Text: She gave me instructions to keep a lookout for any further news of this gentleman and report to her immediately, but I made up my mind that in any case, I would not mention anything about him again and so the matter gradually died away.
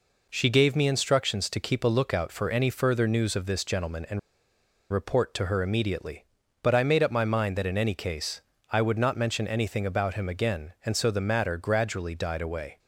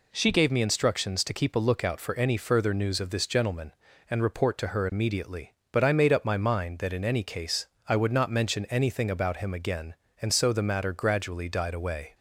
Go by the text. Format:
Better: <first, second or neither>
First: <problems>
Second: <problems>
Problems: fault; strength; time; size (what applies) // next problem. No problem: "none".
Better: second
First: pauses between "and" and "report"; noticeable; at 4.1 s; 0.72 s long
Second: none